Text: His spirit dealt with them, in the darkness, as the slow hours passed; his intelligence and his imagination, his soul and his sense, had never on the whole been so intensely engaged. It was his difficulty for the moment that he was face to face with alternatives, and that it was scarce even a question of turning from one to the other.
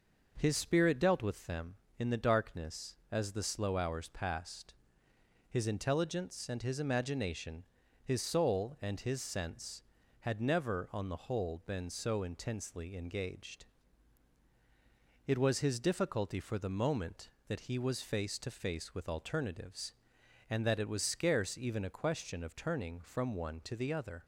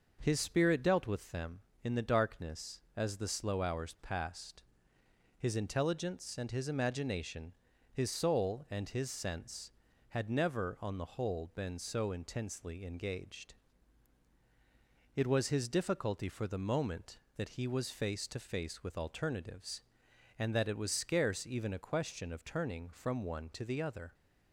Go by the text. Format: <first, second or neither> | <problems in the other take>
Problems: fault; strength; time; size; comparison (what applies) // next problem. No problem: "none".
neither | none